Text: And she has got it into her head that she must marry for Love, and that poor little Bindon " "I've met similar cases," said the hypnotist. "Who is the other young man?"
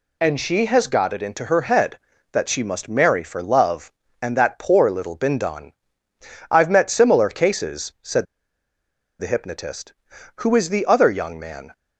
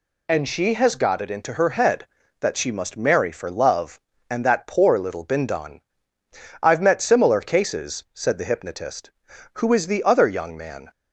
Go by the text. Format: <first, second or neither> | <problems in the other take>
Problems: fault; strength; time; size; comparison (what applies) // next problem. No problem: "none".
second | pauses between "said" and "the"; noticeable; at 8.2 s; 0.95 s long